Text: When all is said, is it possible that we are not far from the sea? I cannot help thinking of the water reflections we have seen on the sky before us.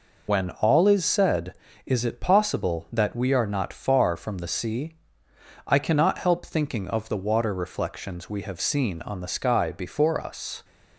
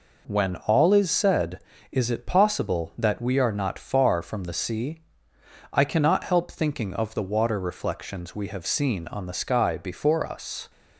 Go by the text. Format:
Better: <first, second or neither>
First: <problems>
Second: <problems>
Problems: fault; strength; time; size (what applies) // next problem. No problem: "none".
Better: second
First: loses the start of "When"; at 0.2 s; 85 ms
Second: none